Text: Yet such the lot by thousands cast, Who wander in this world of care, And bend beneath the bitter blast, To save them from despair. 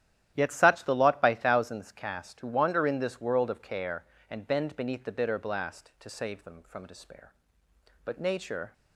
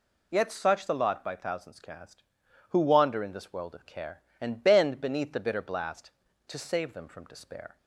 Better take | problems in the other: second | starts louder than the rest; strong; until 1.3 s; 11.5 dB // goes on to say "But Nature"; noticeable; from 8.0 s on; 0.68 s long

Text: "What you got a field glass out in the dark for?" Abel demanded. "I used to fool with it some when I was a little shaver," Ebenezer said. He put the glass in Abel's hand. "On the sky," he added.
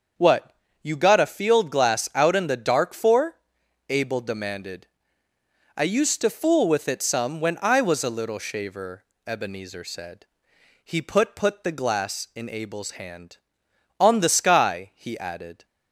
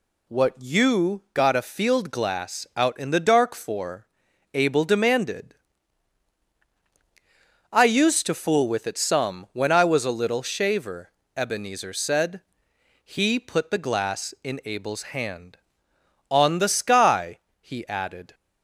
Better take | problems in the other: second | starts louder than the rest; until 1.4 s; 6.5 dB // pauses between "What" and "you"; slight; at 0.5 s; 0.28 s long // says "put" twice; at 11.3 s

